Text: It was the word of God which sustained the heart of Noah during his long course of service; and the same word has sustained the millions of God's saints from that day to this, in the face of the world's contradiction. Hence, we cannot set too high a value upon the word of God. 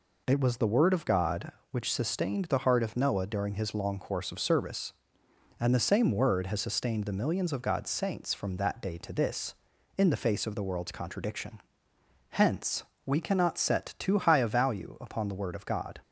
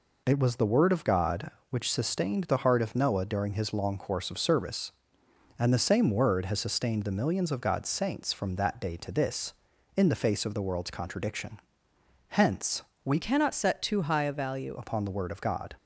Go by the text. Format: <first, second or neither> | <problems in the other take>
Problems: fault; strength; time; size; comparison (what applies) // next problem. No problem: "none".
first | changes voice from "cannot" to "value"; from 13.1 to 14.7 s; 1.6 s long